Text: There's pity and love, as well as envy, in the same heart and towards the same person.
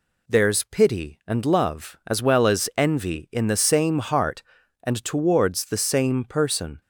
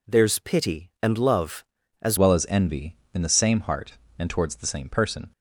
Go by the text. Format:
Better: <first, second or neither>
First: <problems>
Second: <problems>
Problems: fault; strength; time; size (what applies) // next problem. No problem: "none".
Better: first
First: none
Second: changes voice at "well"; from 2.1 s on; 3.2 s long